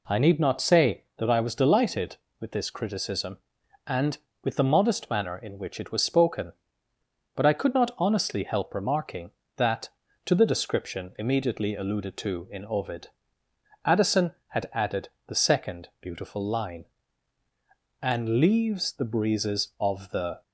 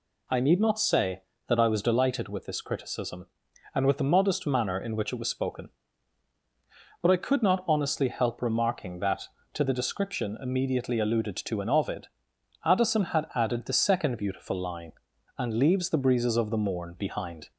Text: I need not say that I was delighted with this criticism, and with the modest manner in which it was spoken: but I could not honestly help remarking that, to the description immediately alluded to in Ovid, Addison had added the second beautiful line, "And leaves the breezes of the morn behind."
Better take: second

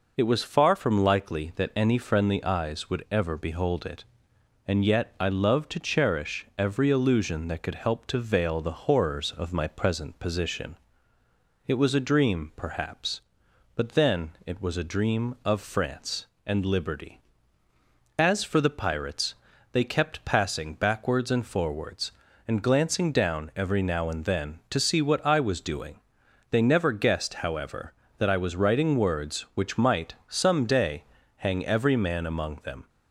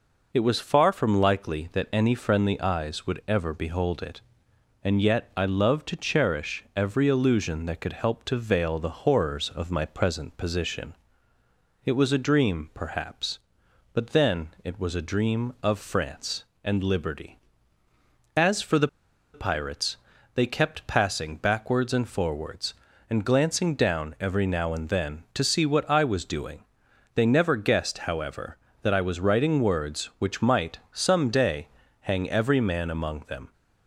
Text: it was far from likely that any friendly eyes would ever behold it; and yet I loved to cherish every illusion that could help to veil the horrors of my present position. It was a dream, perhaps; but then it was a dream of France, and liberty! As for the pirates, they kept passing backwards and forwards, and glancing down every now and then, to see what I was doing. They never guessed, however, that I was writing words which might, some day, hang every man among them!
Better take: first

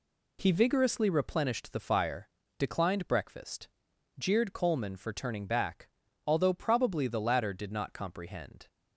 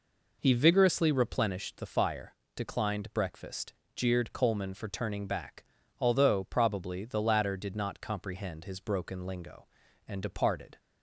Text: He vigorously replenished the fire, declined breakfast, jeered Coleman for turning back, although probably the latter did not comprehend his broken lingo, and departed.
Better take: second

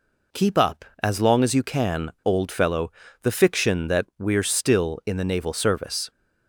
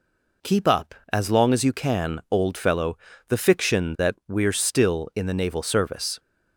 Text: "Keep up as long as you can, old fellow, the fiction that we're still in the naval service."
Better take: neither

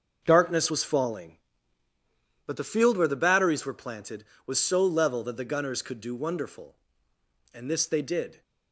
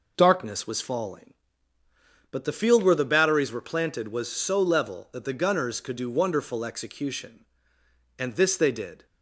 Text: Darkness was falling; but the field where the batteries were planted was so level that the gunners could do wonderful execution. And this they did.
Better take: second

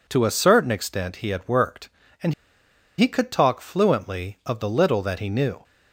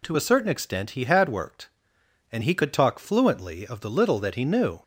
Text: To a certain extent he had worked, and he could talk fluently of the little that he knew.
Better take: second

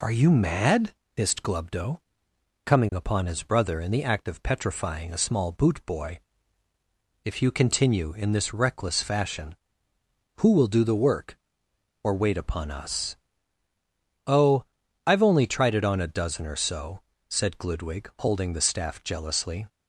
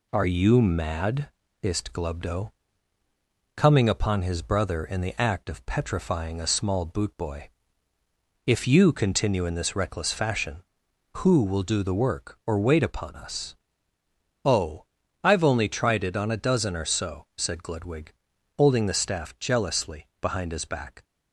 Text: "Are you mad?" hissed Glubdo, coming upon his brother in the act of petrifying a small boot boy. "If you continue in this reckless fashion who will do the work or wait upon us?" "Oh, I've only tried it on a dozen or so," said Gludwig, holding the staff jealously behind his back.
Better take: second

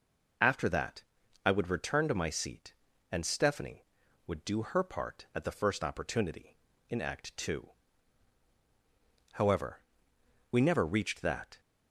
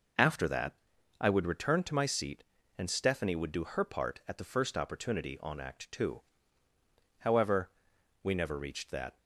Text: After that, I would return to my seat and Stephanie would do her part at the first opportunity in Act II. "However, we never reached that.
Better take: first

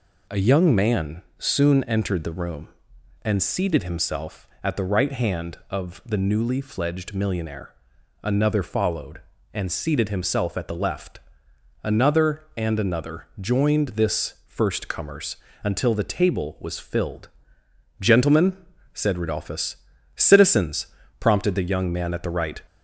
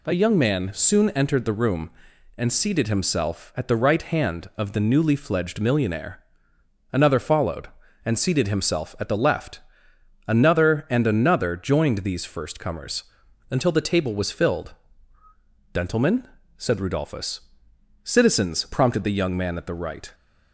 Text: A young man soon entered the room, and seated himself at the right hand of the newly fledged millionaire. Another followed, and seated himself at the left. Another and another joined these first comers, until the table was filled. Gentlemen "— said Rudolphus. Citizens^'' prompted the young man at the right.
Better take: second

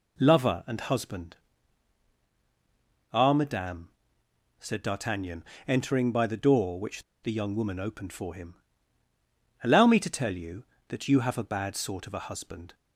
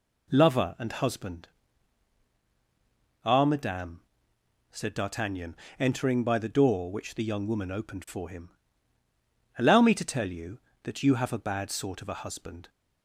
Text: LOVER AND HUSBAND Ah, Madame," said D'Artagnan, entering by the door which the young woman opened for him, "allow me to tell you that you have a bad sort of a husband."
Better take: second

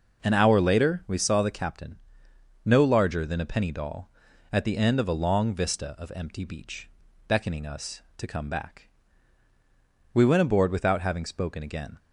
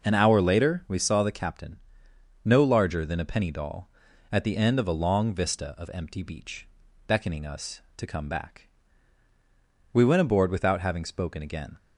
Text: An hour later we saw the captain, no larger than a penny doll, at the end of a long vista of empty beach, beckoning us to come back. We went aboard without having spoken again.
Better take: neither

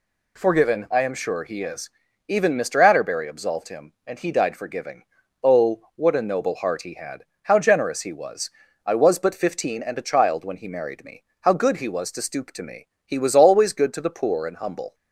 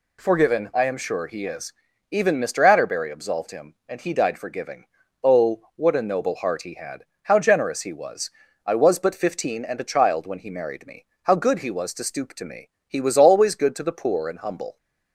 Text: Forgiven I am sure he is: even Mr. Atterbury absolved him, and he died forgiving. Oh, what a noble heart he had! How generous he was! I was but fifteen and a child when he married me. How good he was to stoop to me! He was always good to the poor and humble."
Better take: neither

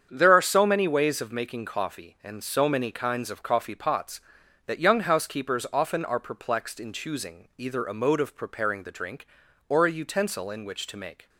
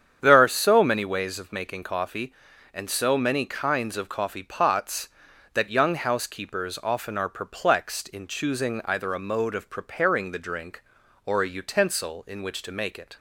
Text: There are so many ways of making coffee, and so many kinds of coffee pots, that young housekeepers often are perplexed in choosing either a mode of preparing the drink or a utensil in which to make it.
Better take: second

